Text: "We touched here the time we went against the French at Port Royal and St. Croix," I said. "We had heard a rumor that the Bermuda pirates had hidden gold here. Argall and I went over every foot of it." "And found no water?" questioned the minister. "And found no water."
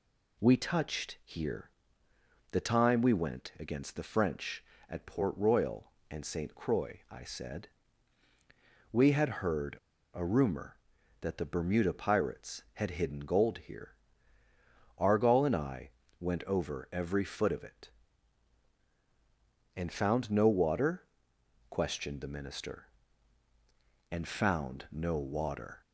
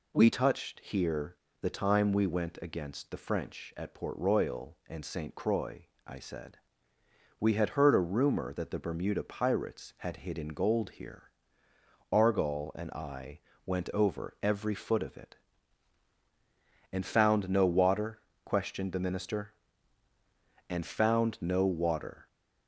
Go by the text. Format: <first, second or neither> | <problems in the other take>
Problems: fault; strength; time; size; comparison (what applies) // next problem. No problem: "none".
second | pauses between "here" and "the"; noticeable; at 1.6 s; 0.82 s long; slight in the second // pauses between "heard" and "a"; slight; at 9.7 s; 0.35 s long // pauses between "I" and "went"; slight; at 15.9 s; 0.30 s long; slight in the second